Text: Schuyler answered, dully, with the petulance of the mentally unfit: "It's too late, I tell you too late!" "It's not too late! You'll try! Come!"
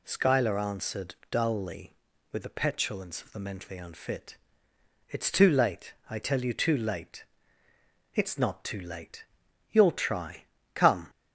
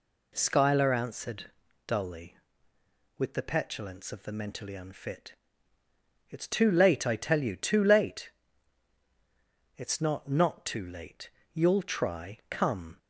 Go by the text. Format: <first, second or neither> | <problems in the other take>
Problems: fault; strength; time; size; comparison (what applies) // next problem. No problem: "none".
first | says "not" twice; at 10.2 s